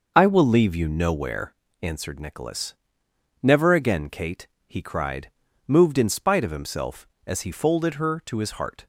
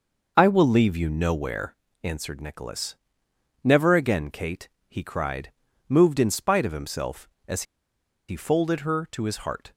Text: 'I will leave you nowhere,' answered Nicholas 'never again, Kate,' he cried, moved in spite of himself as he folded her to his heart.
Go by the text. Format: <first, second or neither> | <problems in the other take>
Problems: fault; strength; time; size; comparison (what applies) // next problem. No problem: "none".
first | pauses between "Nicholas" and "never"; noticeable; at 2.9 s; 0.72 s long; noticeable in the first // pauses between "as" and "he"; noticeable; at 7.6 s; 0.65 s long